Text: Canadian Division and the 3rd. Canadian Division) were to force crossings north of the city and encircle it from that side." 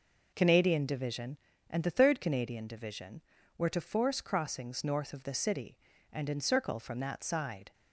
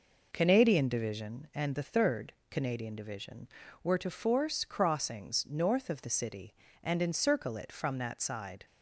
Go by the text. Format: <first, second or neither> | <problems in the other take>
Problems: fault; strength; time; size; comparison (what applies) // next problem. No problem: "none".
second | skips "it"; at 6.7 s